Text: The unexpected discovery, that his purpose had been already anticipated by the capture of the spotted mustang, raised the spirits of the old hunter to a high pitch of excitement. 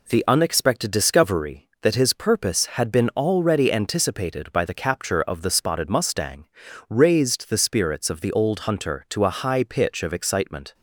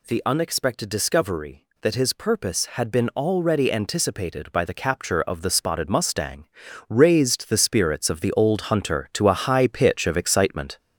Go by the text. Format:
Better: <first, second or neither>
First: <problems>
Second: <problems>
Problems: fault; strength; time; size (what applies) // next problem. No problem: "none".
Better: first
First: none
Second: gets louder; noticeable; throughout; 4.5 dB